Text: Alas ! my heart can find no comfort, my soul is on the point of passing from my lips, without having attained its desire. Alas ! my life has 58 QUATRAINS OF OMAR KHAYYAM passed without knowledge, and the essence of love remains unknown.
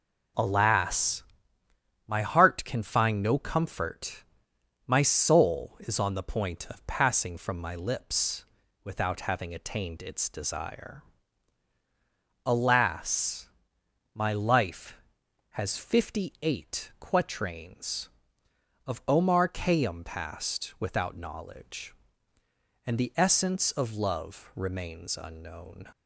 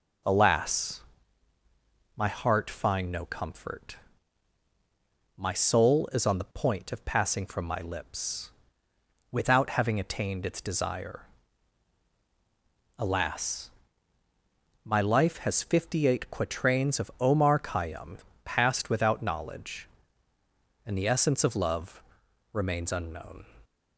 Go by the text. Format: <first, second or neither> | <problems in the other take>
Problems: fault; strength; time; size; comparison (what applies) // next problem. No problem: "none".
first | skips "can"; at 2.7 s // pauses between "KHAYYAM" and "passed"; slight; at 18.1 s; 0.26 s long // pauses between "love" and "remains"; noticeable; at 22.0 s; 0.50 s long